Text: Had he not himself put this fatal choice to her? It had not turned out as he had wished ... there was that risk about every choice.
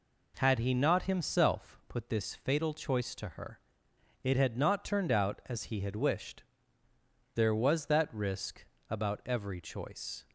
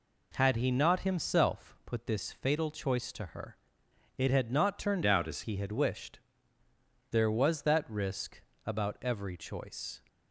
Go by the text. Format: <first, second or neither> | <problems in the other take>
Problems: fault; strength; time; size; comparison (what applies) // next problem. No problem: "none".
first | changes voice from "out" to "as"; from 5.0 to 5.4 s; 0.4 s long // pauses between "risk" and "about"; slight; at 8.4 s; 0.24 s long; slight in the first